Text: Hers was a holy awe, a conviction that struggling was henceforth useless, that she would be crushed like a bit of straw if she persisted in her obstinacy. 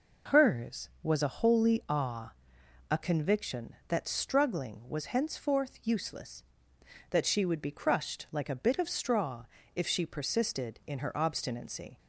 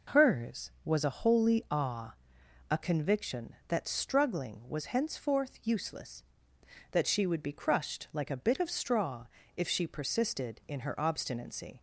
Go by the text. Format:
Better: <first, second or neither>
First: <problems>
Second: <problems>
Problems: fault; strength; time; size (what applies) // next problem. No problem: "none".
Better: neither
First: pauses between "straw" and "if"; slight; at 9.4 s; 0.32 s long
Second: pauses between "straw" and "if"; slight; at 9.2 s; 0.32 s long